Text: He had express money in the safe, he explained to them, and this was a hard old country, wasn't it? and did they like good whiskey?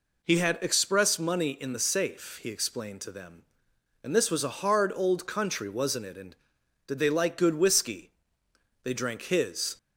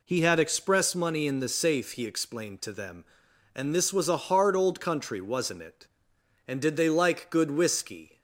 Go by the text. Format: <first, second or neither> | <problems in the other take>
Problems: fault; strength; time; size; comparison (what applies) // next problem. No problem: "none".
second | goes on to say "They drank his"; noticeable; from 8.8 s on; 0.94 s long